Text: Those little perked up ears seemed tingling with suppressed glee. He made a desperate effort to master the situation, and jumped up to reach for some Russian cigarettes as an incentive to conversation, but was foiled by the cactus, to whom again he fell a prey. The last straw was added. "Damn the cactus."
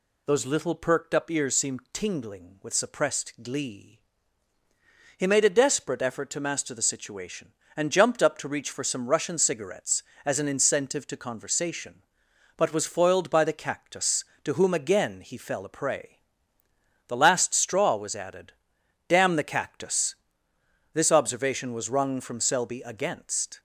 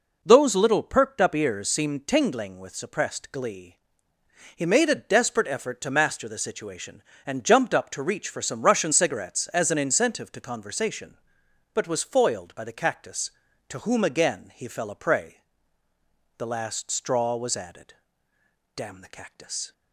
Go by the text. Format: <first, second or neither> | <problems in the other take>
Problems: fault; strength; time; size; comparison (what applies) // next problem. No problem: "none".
second | goes on to say "This observation was wrung from Selby against"; strong; from 20.9 s on; 2.6 s long